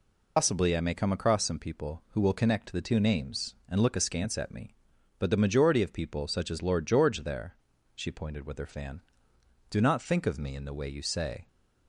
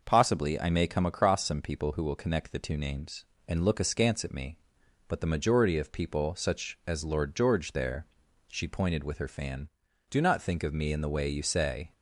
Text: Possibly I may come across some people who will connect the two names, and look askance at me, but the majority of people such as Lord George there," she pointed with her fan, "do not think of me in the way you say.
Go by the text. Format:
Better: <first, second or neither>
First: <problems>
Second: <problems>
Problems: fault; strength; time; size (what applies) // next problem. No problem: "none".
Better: second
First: loses the start of "Possibly"; at 0.3 s; 165 ms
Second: none